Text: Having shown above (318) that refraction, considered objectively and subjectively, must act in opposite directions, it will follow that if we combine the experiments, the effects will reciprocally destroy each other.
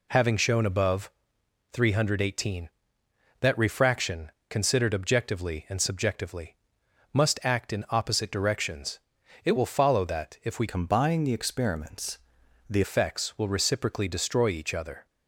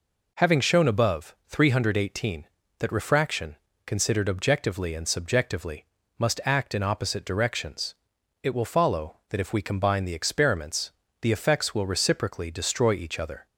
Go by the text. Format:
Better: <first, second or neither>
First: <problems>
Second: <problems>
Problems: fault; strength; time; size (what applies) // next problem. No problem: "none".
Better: second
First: changes voice from "combine" to "the"; from 10.6 to 12.8 s; 2.2 s long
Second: none